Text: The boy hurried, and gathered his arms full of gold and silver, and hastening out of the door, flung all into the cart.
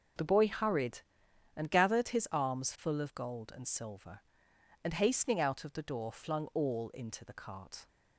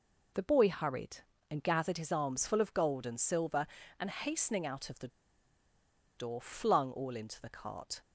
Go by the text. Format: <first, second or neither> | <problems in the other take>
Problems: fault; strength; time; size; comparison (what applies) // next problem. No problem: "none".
first | pauses between "the" and "door"; at 5.0 s; 1.0 s long